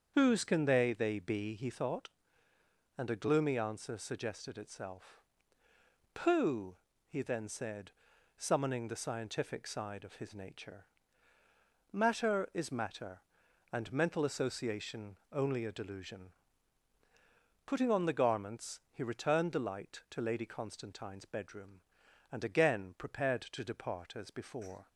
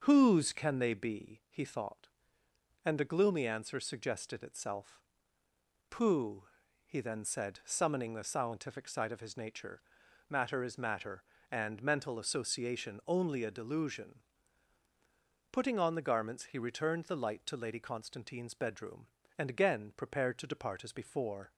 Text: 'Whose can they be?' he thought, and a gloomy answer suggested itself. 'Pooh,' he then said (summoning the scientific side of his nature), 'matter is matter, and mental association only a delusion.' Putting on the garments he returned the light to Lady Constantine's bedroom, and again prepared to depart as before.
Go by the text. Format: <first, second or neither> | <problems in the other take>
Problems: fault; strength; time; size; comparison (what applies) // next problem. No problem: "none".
second | starts louder than the rest; strong; until 1.1 s; 7 dB; also in the second // says "they" twice; at 0.9 s // pauses between "association" and "only"; slight; at 15.1 s; 0.16 s long